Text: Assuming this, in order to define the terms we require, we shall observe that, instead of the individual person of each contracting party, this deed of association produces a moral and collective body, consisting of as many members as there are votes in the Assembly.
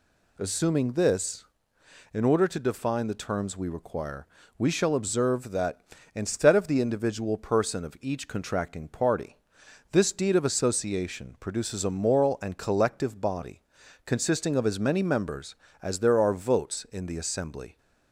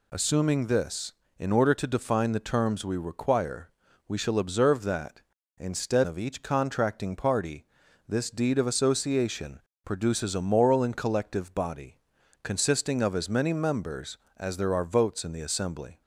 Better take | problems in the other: first | skips "of the individual person"; at 6.0 s // pauses between "association" and "produces"; slight; at 9.5 s; 0.26 s long

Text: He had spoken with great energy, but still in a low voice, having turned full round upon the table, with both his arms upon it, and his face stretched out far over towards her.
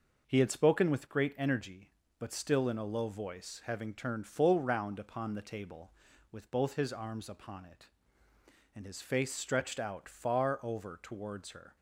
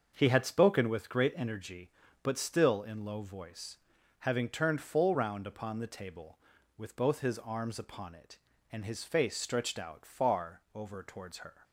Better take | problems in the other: first | starts louder than the rest; until 1.1 s; 6.5 dB // skips "a"; at 3.0 s

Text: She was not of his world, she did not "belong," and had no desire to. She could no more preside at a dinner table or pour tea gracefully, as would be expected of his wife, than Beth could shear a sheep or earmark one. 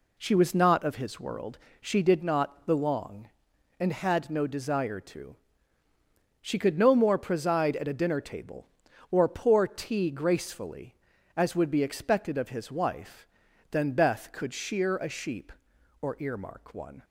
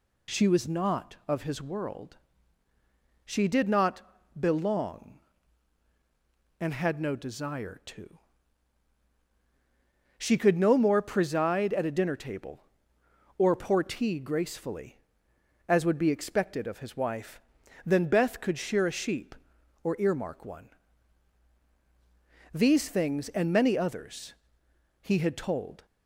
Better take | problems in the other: first | pauses between "not" and "belong"; slight; at 4.0 s; 0.36 s long // goes on to say "These things and many others he had told"; strong; from 22.5 s on; 3.3 s long

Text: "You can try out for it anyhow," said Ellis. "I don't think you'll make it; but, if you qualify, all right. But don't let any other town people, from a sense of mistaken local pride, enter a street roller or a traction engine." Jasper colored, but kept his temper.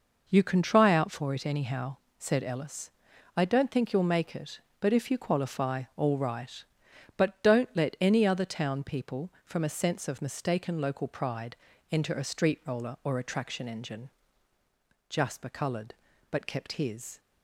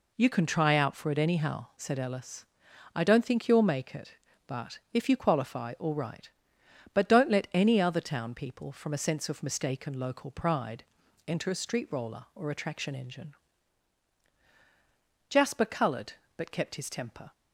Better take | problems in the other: second | stops before "temper"; at 17.1 s

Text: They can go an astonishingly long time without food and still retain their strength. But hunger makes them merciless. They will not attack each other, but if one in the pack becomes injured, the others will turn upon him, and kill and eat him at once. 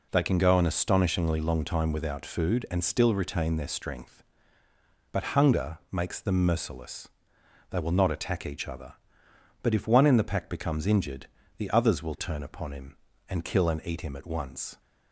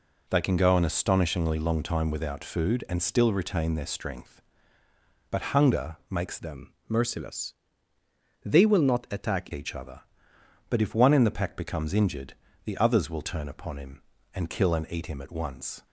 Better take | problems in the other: first | changes voice from "them" to "attack"; from 6.3 to 9.4 s; 3.1 s long // pauses between "them" and "merciless"; slight; at 6.7 s; 0.16 s long

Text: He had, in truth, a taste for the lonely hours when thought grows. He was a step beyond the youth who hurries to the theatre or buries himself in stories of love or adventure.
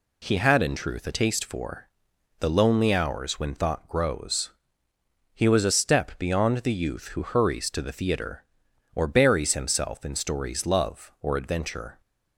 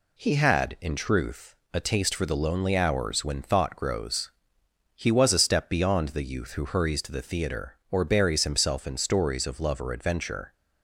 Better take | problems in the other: second | pauses between "for" and "the"; noticeable; at 1.8 s; 0.54 s long // skips "of"; at 10.6 s

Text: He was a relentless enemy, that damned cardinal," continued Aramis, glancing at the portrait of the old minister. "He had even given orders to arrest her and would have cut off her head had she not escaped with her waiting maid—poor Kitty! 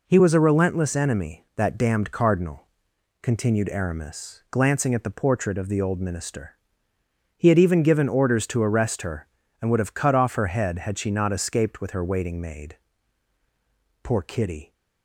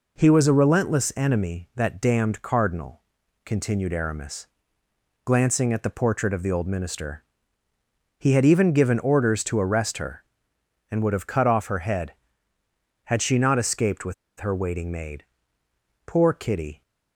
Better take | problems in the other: first | pauses between "with" and "her"; slight; at 14.1 s; 0.25 s long

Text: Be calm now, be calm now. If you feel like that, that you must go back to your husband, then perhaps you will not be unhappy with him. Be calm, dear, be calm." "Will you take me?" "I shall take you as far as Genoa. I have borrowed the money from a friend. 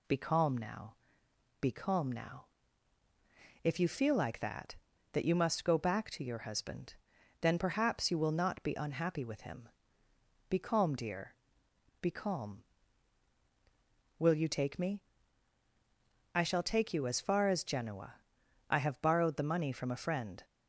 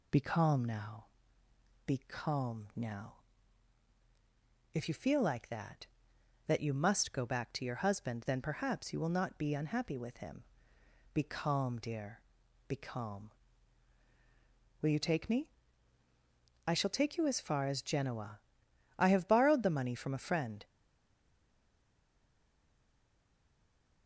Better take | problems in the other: first | stays silent after the last word; strong; from 20.6 s on; 3.4 s long

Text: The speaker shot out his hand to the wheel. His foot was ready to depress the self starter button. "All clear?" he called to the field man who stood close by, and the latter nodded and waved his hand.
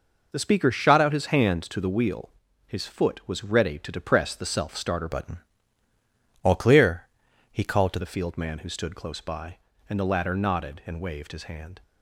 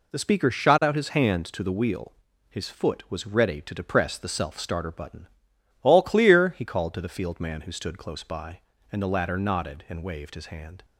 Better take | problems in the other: second | changes voice from "button" to "to"; from 5.1 to 7.9 s; 2.8 s long

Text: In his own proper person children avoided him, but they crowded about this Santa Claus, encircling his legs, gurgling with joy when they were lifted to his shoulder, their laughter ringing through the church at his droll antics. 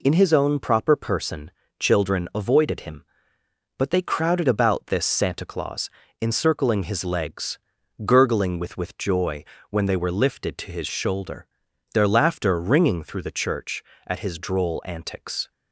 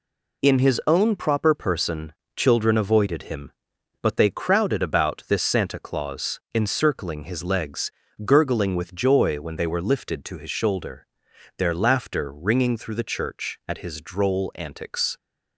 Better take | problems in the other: second | pauses between "person" and "children"; slight; at 1.5 s; 0.28 s long; slight in the second // says "with" twice; at 8.7 s // pauses between "joy" and "when"; slight; at 9.4 s; 0.24 s long

